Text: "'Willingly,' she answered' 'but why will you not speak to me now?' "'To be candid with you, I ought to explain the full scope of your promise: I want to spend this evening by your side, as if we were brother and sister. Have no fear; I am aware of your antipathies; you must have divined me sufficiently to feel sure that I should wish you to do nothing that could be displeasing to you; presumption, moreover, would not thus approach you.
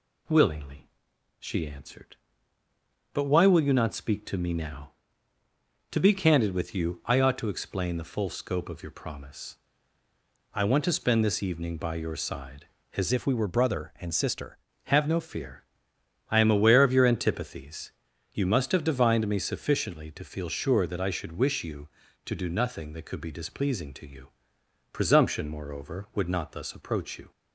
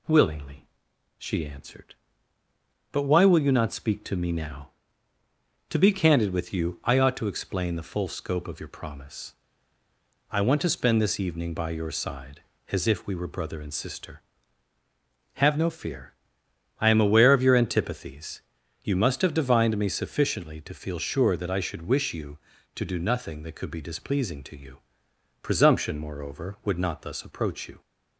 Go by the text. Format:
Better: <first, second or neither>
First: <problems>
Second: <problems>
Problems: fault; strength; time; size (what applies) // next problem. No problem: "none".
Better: second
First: changes voice from "if" to "sister"; from 13.1 to 14.5 s; 1.4 s long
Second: none